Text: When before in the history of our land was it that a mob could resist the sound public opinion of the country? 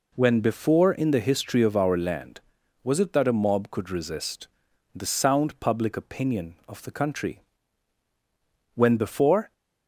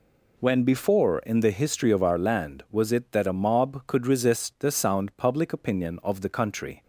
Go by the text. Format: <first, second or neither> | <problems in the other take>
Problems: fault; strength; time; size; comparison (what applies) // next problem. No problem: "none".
second | pauses between "resist" and "the"; noticeable; at 4.4 s; 0.48 s long // goes on to say "When before"; noticeable; from 8.7 s on; 0.78 s long